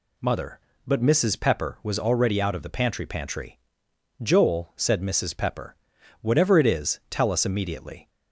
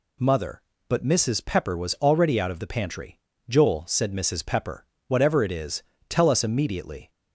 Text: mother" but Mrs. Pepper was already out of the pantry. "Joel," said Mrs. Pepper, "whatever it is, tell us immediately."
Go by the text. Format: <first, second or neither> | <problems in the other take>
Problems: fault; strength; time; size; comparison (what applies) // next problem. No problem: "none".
second | says "pantry" twice; at 3.0 s